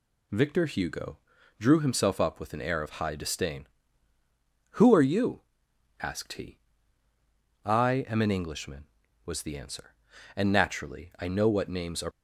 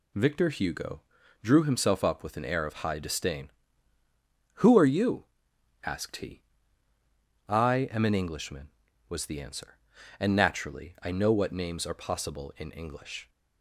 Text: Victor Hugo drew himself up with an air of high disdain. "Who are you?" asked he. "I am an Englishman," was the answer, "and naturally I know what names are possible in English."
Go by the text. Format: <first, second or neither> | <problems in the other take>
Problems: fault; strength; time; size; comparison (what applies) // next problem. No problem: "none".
second | pauses between "Hugo" and "drew"; at 1.1 s; 0.42 s long; also in the second // stops before "possible in English"; at 12.1 s